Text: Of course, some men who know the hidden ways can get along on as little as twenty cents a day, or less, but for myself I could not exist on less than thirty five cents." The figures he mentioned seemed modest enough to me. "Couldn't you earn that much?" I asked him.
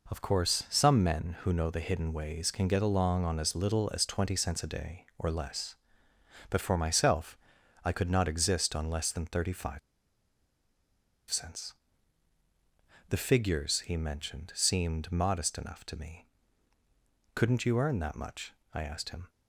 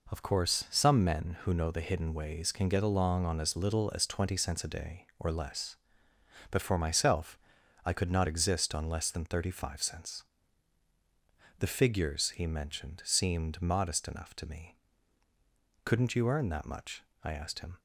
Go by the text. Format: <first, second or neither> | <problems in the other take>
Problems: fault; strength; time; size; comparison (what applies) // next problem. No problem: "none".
second | pauses between "myself" and "I"; noticeable; at 7.3 s; 0.46 s long; noticeable in the second // pauses between "five" and "cents"; strong; at 9.7 s; 1.5 s long